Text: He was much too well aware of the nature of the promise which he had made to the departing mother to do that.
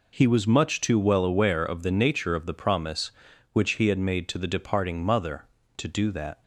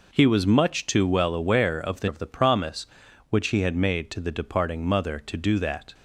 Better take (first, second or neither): first